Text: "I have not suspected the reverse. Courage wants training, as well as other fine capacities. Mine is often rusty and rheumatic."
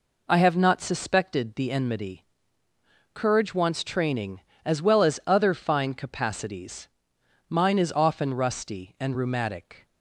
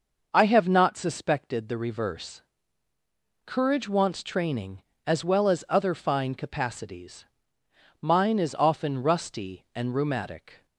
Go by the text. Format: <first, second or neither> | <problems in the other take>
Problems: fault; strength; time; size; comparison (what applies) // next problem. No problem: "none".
second | says "enmity" for "reverse"; at 1.7 s